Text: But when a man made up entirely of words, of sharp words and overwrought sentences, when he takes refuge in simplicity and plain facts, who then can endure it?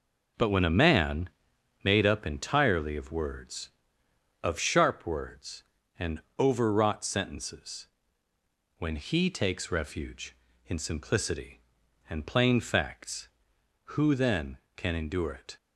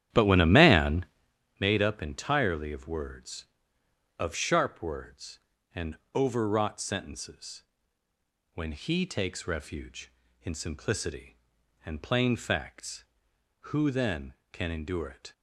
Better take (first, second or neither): first